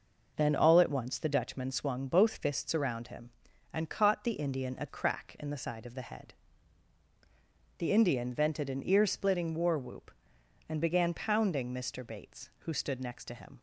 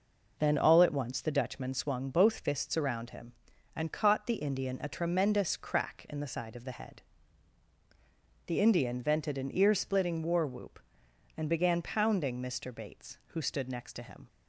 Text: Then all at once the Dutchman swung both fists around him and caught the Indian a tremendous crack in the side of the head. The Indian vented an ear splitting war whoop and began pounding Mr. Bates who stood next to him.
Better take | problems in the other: second | skips "tremendous"; at 4.8 s

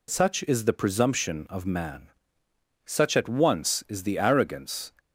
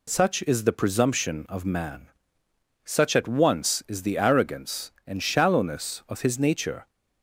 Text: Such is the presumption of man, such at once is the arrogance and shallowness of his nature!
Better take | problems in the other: second | stops before "and shallowness of his nature"; at 4.9 s

